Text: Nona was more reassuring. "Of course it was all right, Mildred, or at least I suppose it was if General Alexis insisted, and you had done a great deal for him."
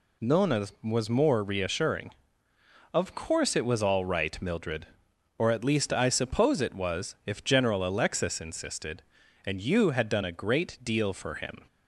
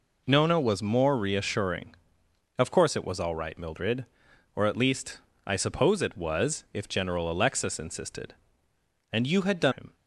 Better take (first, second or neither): first